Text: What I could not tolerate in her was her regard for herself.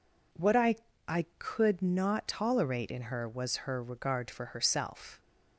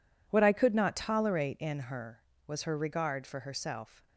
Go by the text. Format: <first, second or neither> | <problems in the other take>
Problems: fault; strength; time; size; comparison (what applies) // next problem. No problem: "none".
second | says "I" twice; at 1.0 s